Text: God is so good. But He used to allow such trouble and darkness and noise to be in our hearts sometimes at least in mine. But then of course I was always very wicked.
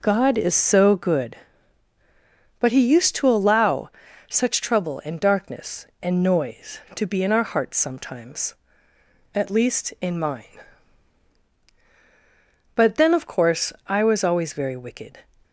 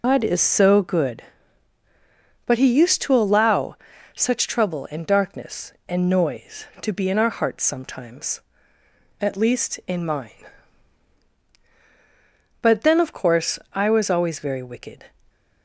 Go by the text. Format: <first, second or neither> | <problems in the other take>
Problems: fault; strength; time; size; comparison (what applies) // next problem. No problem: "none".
first | loses the start of "God"; at 0.0 s; 170 ms // pauses between "allow" and "such"; at 3.7 s; 0.38 s long; also in the first // pauses between "course" and "I"; slight; at 13.5 s; 0.16 s long; slight in the first